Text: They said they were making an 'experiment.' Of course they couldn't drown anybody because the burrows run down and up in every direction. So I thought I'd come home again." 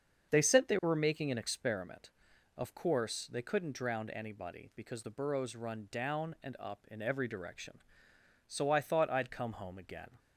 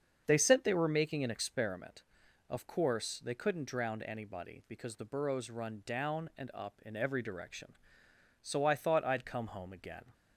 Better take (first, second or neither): neither